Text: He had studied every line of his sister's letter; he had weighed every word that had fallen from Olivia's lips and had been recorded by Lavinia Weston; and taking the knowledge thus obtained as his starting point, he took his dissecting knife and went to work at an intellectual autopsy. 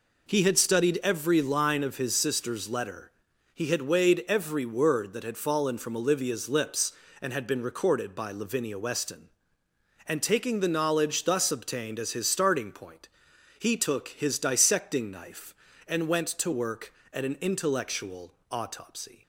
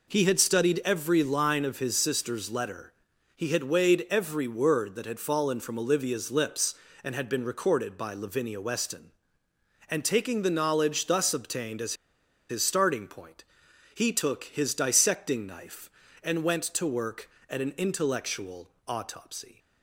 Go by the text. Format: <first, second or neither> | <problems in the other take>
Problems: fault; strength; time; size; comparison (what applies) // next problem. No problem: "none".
first | pauses between "as" and "his"; noticeable; at 11.9 s; 0.56 s long // pauses between "intellectual" and "autopsy"; slight; at 18.6 s; 0.18 s long; slight in the first